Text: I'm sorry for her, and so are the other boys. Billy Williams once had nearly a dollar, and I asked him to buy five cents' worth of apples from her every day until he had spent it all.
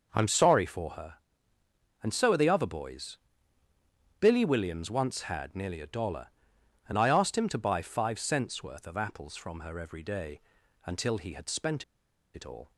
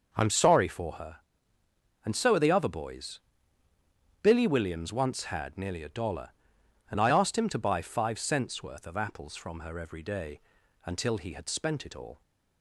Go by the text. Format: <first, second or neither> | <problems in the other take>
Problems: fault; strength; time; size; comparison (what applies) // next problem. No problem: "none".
second | pauses between "day" and "until"; at 10.3 s; 0.44 s long; also in the second // pauses between "spent" and "it"; noticeable; at 11.8 s; 0.51 s long